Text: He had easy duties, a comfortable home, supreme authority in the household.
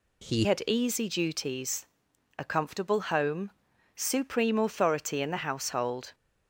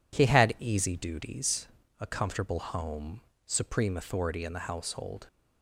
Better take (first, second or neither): second